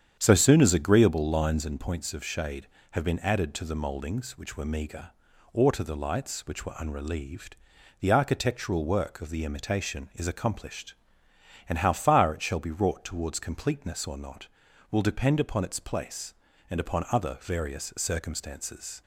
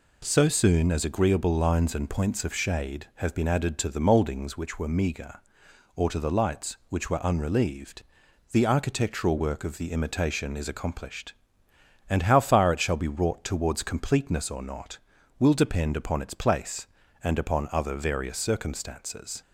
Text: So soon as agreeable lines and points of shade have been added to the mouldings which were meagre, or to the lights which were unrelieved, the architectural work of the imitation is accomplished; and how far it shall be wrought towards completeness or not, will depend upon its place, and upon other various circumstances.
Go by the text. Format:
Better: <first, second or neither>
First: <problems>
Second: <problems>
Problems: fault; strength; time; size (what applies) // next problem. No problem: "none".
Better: second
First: starts louder than the rest; strong; until 1.8 s; 8.5 dB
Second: none